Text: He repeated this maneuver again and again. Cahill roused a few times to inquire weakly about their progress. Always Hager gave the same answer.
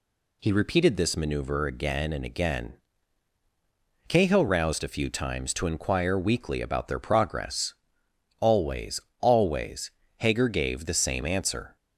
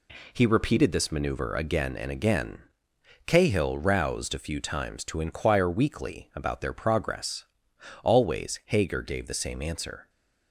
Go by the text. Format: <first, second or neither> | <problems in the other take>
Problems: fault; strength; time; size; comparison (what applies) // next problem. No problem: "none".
second | says "Always" twice; at 9.1 s